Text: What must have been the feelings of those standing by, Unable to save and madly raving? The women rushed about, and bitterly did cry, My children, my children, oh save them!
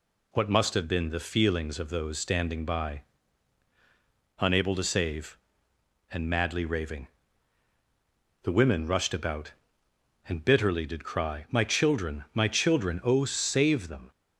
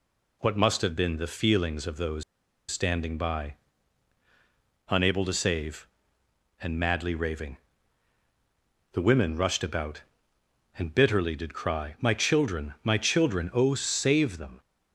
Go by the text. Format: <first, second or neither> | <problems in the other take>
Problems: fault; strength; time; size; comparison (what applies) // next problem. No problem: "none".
first | pauses between "those" and "standing"; noticeable; at 2.2 s; 0.46 s long